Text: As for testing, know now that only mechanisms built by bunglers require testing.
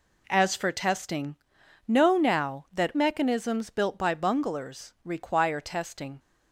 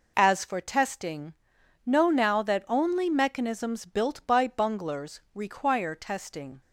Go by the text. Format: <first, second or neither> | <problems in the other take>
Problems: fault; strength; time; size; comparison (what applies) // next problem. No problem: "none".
second | skips "only"; at 2.9 s